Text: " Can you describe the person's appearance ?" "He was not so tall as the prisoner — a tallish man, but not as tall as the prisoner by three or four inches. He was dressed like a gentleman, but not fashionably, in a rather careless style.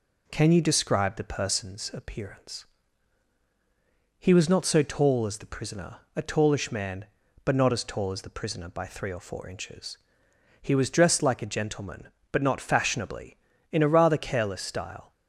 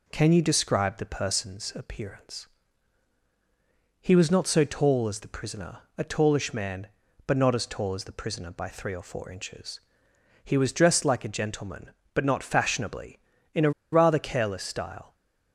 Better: first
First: none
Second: pauses between "a" and "rather"; slight; at 13.7 s; 0.21 s long

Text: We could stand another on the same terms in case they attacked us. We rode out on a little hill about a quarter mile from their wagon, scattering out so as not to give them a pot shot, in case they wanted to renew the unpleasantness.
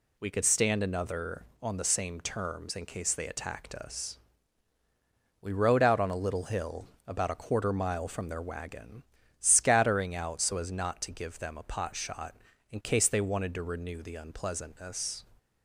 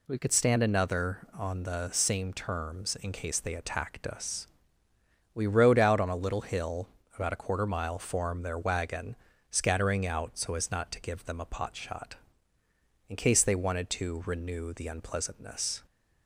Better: first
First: pauses between "hill" and "about"; slight; at 6.8 s; 0.20 s long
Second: pauses between "hill" and "about"; slight; at 6.8 s; 0.26 s long // says "form" for "from"; at 7.9 s

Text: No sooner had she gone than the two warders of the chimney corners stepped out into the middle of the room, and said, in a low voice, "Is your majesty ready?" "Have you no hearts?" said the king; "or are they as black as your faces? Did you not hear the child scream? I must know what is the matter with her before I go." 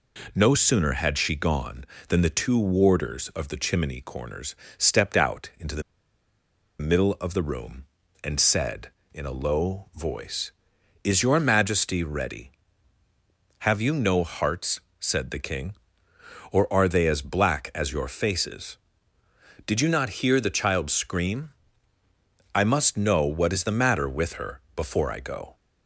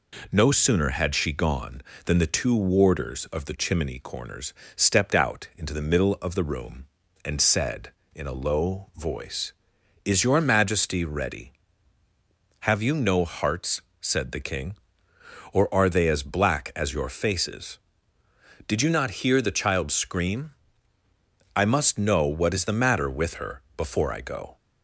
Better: second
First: pauses between "corners" and "stepped"; slight; at 4.5 s; 0.22 s long // pauses between "the" and "middle"; noticeable; at 5.8 s; 0.97 s long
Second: pauses between "corners" and "stepped"; slight; at 4.5 s; 0.22 s long

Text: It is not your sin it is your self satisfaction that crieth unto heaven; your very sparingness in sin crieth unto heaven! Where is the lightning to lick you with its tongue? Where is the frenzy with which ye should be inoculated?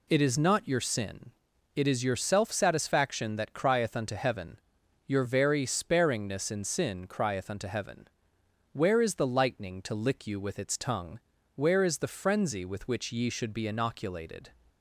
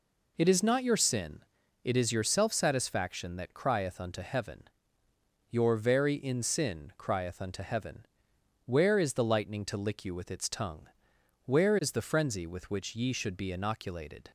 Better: first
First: pauses between "sin" and "it"; at 1.3 s; 0.44 s long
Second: pauses between "sin" and "it"; at 1.4 s; 0.44 s long // skips "sparingness"; at 6.1 s

